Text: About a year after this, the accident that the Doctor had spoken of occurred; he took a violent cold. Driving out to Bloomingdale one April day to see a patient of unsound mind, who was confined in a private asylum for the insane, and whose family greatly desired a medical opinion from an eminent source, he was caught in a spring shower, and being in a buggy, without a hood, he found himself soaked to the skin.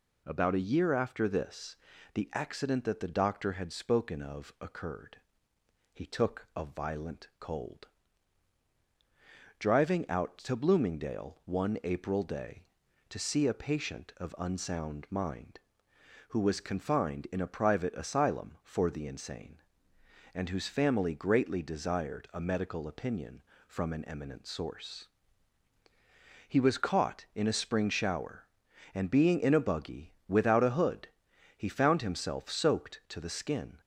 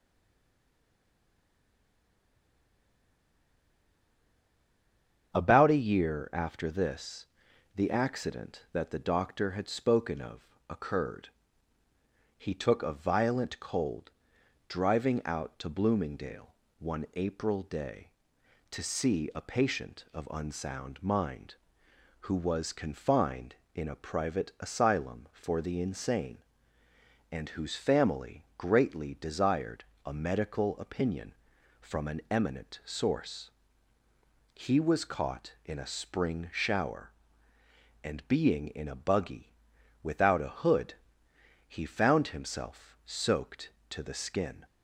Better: first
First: none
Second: stays silent before the first word; strong; until 5.3 s; 5.3 s long // starts louder than the rest; strong; until 6.4 s; 7 dB // pauses between "of" and "occurred"; slight; at 10.4 s; 0.22 s long // pauses between "Bloomingdale" and "one"; slight; at 16.5 s; 0.26 s long // pauses between "desired" and "a"; slight; at 29.8 s; 0.22 s long

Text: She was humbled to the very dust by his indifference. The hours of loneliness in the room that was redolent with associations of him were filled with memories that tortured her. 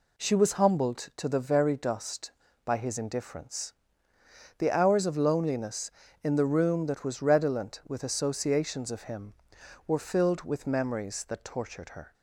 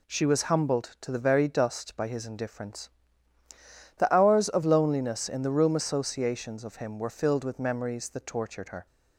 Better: first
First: none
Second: skips "that was redolent with"; at 5.7 s

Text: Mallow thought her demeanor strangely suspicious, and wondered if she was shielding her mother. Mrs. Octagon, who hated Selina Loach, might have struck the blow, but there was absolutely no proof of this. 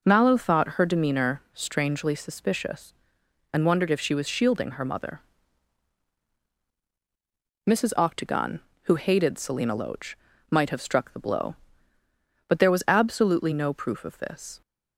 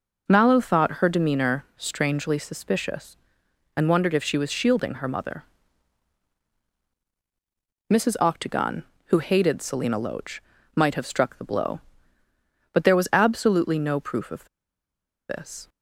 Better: first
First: none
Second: pauses between "of" and "this"; noticeable; at 14.4 s; 0.83 s long

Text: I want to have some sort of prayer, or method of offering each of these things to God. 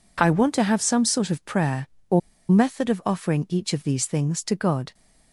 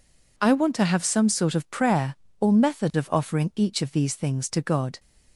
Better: second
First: pauses between "or" and "method"; slight; at 2.2 s; 0.29 s long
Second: none

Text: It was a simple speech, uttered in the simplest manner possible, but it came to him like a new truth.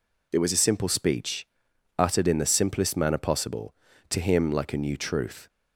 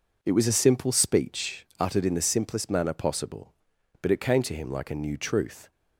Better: second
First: skips "but it came"; at 3.9 s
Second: none

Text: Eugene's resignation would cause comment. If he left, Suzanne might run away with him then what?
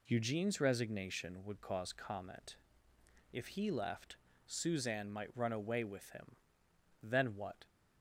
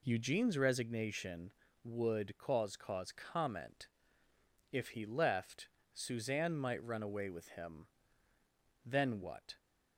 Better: first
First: pauses between "him" and "then"; noticeable; at 6.3 s; 0.66 s long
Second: says "cause" twice; at 2.7 s // pauses between "him" and "then"; noticeable; at 7.8 s; 0.98 s long

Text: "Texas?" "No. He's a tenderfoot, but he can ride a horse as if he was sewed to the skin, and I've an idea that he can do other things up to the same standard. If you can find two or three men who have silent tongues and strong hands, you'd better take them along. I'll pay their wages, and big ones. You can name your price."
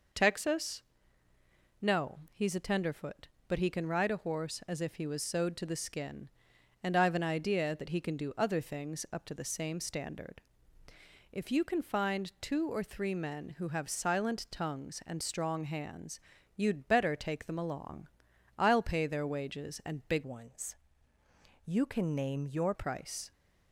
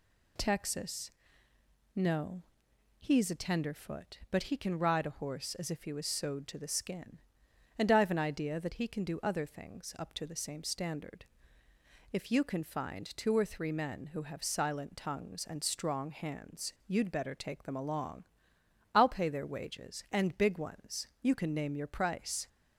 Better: second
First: changes voice from "ones" to "your"; from 20.2 to 22.7 s; 2.5 s long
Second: none

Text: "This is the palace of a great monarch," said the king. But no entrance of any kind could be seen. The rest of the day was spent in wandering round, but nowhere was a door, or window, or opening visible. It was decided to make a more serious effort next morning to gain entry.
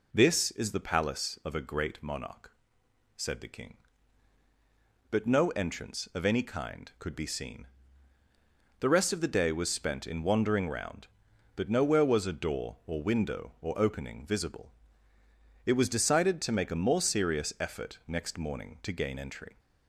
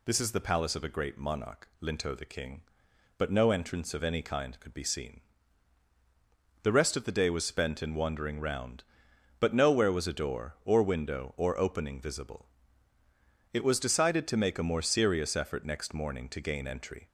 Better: first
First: none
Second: says "linto" for "said"; at 1.8 s

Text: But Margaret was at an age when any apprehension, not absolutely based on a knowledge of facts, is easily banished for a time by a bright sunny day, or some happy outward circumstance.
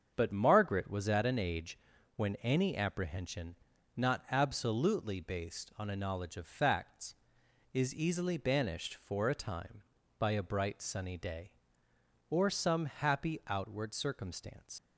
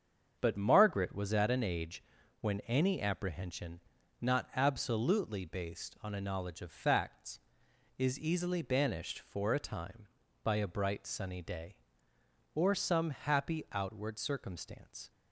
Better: second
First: starts louder than the rest; until 1.1 s; 7 dB // pauses between "age" and "when"; at 1.7 s; 0.38 s long // leaves "circumstance" unfinished; at 14.7 s; 70 ms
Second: starts louder than the rest; until 1.4 s; 7 dB // pauses between "age" and "when"; at 2.0 s; 0.38 s long

